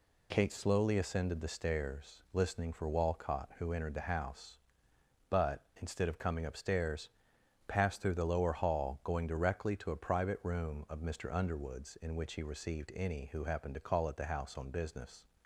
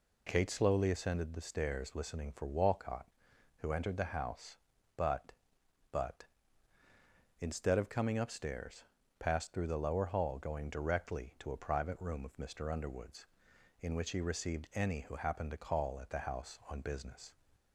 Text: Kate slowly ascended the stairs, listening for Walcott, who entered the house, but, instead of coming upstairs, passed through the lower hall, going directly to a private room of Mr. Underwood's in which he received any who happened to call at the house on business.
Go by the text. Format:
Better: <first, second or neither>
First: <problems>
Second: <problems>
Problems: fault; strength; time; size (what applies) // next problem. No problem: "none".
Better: first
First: none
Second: says "but" twice; at 5.8 s